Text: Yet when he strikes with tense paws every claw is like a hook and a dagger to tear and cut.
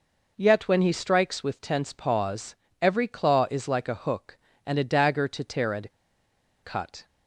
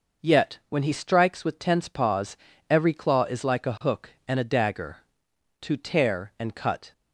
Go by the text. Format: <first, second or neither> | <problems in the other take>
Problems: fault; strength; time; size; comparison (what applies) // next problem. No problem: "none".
second | pauses between "paws" and "every"; slight; at 2.5 s; 0.24 s long; slight in the second // pauses between "and" and "cut"; noticeable; at 5.9 s; 0.72 s long